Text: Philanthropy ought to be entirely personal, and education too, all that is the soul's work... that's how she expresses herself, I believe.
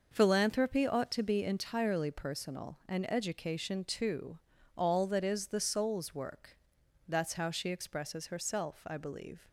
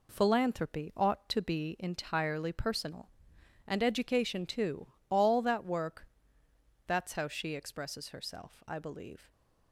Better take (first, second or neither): first